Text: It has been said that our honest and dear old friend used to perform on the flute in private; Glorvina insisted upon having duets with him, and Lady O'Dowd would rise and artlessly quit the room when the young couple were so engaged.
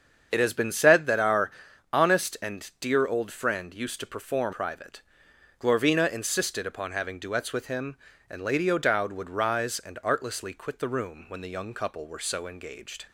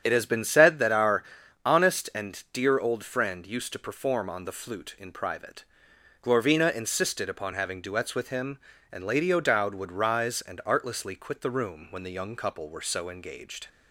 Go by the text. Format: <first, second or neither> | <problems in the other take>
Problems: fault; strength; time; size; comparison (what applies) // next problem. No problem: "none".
second | starts louder than the rest; strong; until 1.3 s; 7 dB; strong in the second // pauses between "our" and "honest"; at 1.5 s; 0.42 s long; also in the second // skips "on the flute in"; at 4.5 s